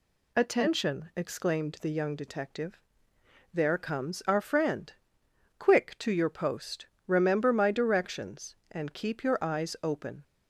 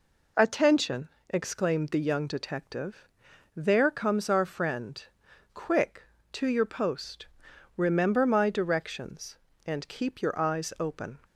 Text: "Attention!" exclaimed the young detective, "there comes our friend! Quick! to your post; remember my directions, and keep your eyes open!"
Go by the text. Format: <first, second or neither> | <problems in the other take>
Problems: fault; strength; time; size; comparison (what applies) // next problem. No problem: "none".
neither | none